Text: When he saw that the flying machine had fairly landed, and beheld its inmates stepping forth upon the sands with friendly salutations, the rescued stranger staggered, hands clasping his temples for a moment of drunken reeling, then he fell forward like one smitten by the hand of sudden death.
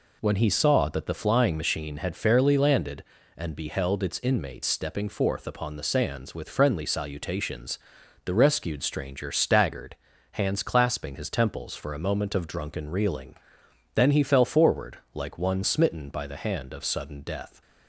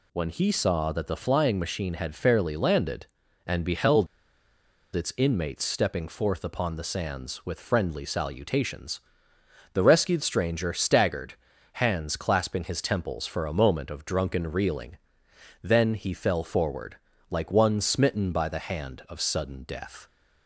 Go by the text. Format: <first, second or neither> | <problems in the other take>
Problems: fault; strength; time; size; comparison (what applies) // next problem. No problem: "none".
first | pauses between "beheld" and "its"; noticeable; at 4.0 s; 0.89 s long // pauses between "forward" and "like"; slight; at 16.9 s; 0.32 s long; slight in the first